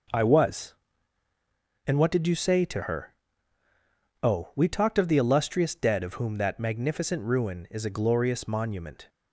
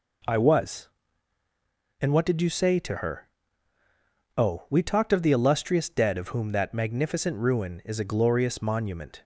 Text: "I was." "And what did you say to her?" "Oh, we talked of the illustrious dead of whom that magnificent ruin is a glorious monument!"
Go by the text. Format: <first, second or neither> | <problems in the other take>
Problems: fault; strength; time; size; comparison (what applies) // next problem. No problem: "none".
second | gets quieter; strong; throughout; 8.5 dB